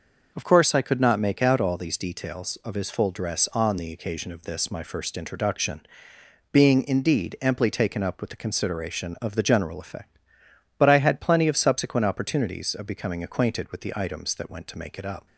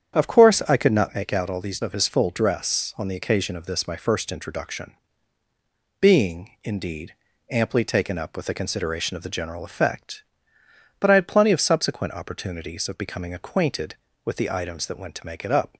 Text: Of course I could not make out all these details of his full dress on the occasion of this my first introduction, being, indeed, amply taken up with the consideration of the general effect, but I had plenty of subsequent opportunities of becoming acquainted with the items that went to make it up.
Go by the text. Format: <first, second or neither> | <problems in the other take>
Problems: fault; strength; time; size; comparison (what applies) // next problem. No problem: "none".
first | starts louder than the rest; strong; until 1.2 s; 8.5 dB // skips "details"; at 1.8 s